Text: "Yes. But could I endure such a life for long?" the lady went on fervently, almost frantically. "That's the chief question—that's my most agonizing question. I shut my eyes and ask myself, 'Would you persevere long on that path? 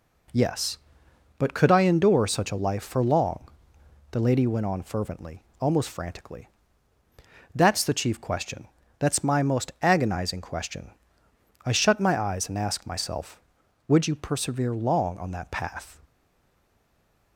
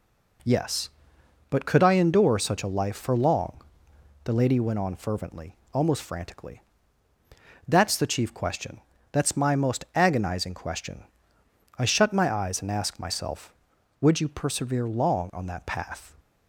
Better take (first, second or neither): second